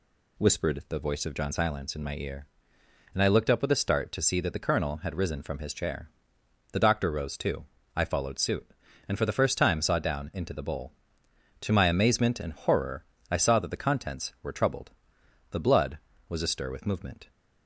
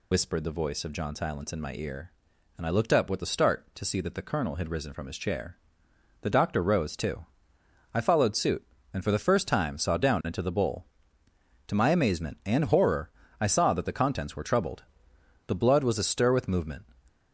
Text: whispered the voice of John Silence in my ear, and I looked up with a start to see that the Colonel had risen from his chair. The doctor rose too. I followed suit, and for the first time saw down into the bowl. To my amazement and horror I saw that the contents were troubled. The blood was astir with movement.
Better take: first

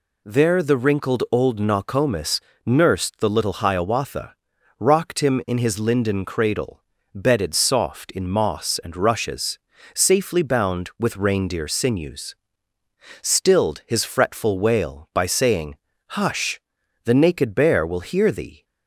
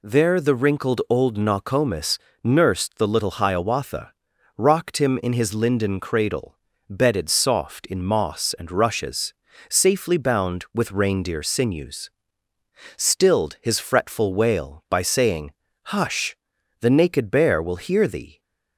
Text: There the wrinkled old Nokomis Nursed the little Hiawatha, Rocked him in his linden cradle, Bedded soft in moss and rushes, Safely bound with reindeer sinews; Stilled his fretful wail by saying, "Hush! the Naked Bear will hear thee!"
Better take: neither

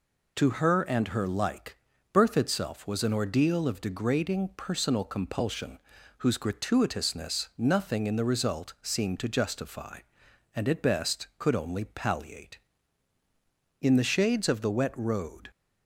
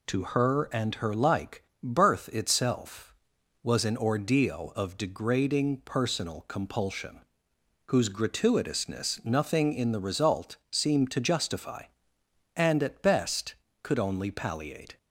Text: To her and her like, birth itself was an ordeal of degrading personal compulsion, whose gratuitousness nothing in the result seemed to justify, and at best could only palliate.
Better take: second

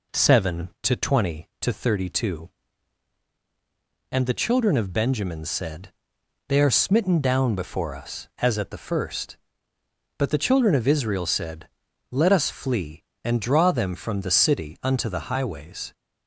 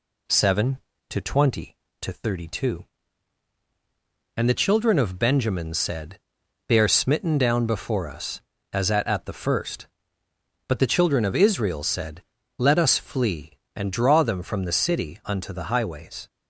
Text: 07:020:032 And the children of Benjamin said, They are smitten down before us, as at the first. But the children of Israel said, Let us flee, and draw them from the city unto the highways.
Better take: first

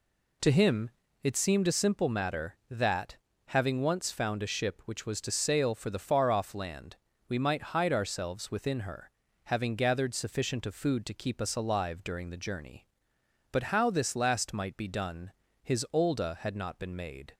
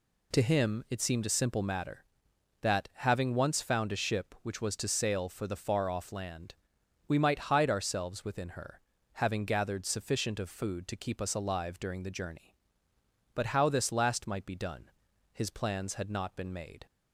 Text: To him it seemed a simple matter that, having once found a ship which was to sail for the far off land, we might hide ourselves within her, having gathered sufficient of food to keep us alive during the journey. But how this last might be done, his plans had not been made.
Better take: second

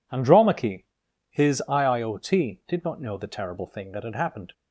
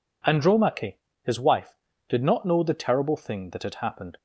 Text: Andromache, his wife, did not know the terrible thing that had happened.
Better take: second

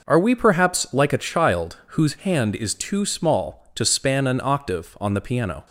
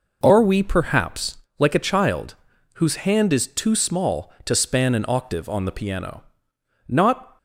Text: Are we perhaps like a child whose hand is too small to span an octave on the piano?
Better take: first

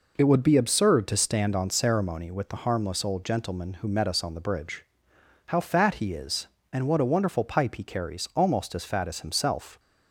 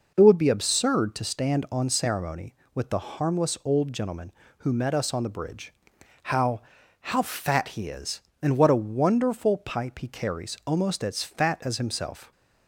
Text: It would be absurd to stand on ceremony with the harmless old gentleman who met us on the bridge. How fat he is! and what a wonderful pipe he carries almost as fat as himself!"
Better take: first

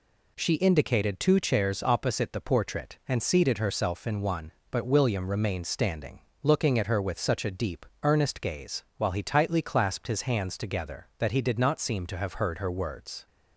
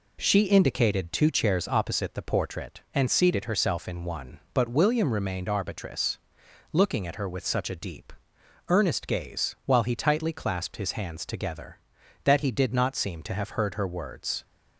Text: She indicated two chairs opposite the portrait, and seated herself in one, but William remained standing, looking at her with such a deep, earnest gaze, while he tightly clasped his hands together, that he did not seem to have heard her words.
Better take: first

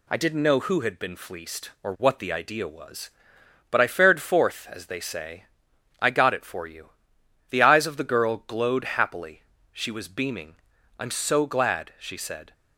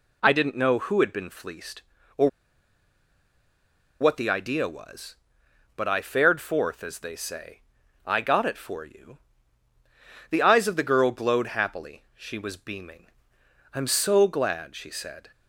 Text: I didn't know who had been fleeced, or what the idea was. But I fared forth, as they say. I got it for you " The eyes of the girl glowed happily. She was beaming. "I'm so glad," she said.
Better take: first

